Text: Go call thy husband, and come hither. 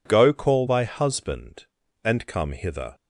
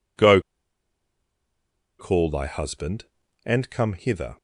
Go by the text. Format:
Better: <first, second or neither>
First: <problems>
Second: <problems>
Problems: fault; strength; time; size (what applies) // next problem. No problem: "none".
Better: first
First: none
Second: pauses between "Go" and "call"; strong; at 0.4 s; 1.5 s long